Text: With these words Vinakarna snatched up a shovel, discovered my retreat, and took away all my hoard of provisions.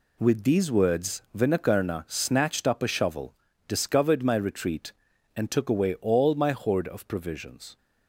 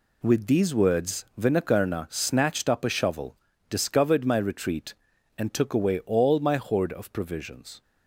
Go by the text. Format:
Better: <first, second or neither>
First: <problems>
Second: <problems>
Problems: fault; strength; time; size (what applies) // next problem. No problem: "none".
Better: neither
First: none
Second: none